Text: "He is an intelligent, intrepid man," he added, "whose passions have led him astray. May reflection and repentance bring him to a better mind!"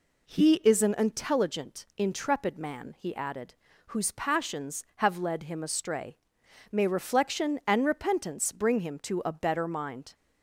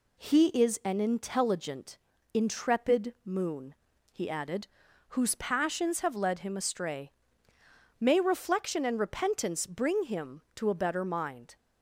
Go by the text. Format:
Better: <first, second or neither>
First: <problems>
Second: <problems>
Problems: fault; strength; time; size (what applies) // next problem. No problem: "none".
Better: first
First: none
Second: says "moon" for "man"; at 3.2 s